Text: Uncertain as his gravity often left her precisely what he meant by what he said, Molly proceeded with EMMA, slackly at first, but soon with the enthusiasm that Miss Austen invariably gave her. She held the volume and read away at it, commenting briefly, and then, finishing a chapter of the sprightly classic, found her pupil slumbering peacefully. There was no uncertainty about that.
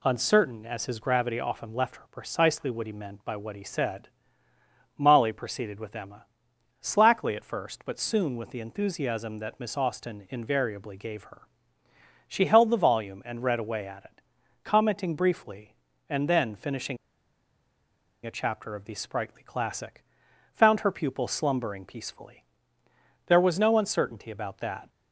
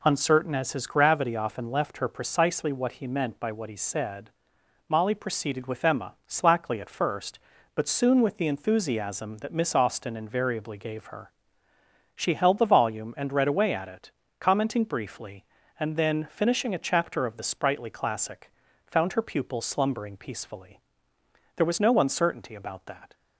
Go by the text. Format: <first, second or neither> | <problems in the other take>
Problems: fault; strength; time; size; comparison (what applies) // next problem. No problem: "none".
second | pauses between "finishing" and "a"; strong; at 16.9 s; 1.2 s long